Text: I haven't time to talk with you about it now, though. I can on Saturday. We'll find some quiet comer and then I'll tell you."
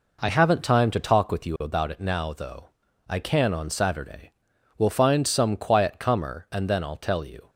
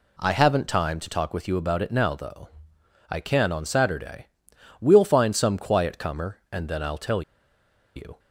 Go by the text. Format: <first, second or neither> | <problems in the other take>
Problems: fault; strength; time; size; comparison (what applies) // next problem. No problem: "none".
first | pauses between "tell" and "you"; noticeable; at 7.2 s; 0.75 s long